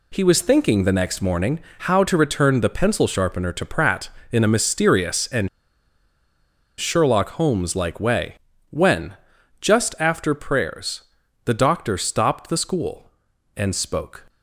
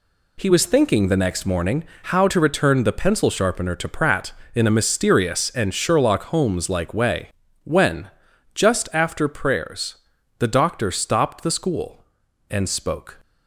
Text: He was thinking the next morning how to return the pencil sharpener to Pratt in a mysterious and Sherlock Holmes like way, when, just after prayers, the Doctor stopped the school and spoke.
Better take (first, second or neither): second